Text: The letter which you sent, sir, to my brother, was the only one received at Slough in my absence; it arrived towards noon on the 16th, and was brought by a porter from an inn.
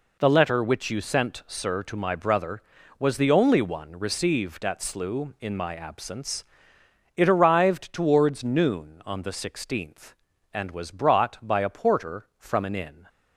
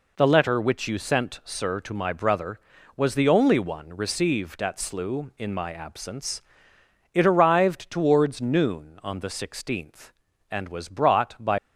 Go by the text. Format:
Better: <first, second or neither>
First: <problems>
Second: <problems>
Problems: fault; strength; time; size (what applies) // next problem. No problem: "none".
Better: first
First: none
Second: stops before "a porter from an inn"; at 11.5 s